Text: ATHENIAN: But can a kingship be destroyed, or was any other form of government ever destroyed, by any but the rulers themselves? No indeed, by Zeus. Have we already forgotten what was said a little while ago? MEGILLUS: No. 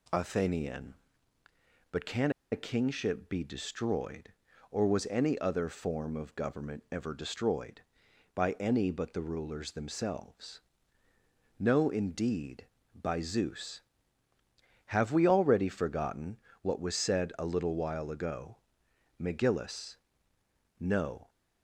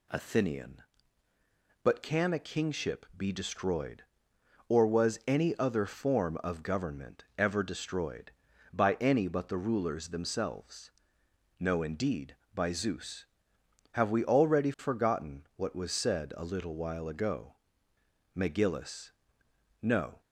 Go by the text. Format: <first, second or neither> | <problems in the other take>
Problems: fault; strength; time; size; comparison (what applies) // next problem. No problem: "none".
second | pauses between "can" and "a"; slight; at 2.3 s; 0.20 s long // pauses between "forgotten" and "what"; slight; at 16.3 s; 0.22 s long